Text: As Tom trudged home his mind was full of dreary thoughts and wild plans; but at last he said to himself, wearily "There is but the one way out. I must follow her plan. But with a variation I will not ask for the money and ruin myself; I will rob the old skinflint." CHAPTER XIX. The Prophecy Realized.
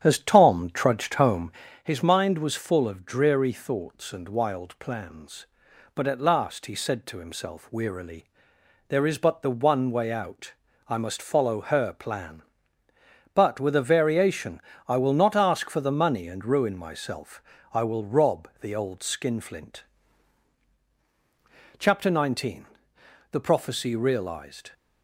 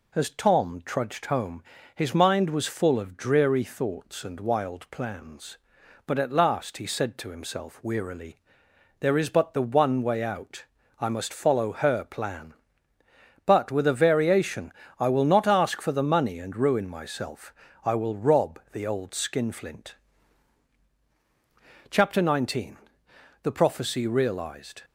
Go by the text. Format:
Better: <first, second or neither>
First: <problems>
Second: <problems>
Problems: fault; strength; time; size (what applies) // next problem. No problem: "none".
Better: second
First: starts louder than the rest; strong; until 1.8 s; 10 dB // pauses between "home" and "his"; slight; at 1.5 s; 0.32 s long // pauses between "wearily" and "There"; noticeable; at 8.2 s; 0.64 s long // pauses between "variation" and "I"; slight; at 14.6 s; 0.26 s long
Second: pauses between "home" and "his"; slight; at 1.6 s; 0.32 s long // pauses between "wearily" and "There"; noticeable; at 8.3 s; 0.64 s long // pauses between "variation" and "I"; slight; at 14.7 s; 0.26 s long